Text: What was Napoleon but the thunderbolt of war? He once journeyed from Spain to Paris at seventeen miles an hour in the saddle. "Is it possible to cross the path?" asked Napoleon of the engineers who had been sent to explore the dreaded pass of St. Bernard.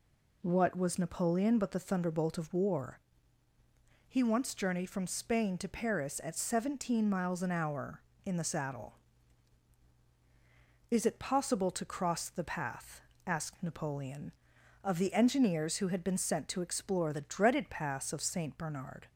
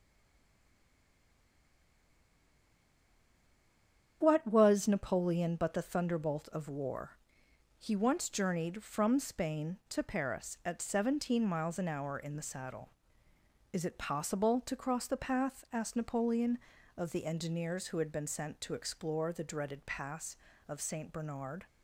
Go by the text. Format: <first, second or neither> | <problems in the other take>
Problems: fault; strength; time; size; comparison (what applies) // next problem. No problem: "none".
first | stays silent before the first word; strong; until 4.2 s; 4.2 s long // starts louder than the rest; strong; until 5.2 s; 8.5 dB